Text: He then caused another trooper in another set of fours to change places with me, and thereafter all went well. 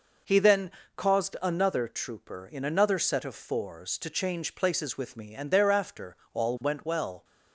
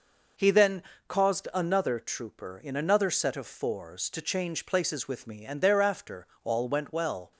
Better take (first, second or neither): neither